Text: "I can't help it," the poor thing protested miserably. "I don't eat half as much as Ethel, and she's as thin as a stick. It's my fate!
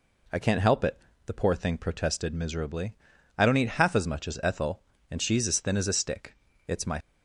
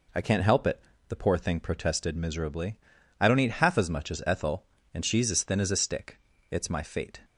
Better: second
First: stops before "fate"; at 6.9 s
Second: none

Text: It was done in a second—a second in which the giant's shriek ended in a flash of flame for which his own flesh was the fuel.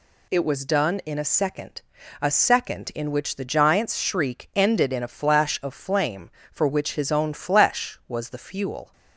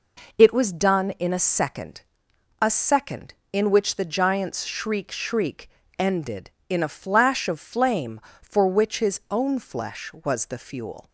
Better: first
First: none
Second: says "shriek" twice; at 5.1 s

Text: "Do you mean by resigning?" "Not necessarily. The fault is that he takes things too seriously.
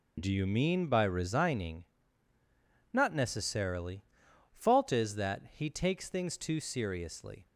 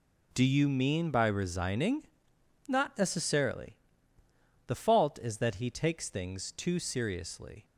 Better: second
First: skips "The"; at 4.2 s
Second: none

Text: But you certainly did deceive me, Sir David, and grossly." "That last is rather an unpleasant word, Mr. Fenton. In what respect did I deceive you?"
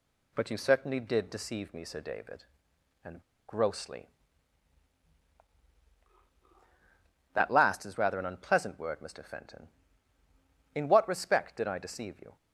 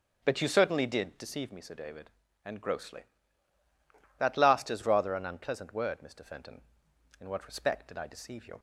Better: second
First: pauses between "and" and "grossly"; slight; at 3.2 s; 0.26 s long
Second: none

